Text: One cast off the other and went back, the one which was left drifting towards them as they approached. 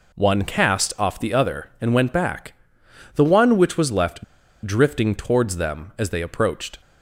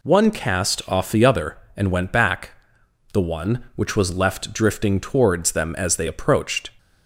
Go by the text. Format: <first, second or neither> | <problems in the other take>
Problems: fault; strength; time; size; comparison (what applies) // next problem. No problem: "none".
second | pauses between "left" and "drifting"; at 4.2 s; 0.42 s long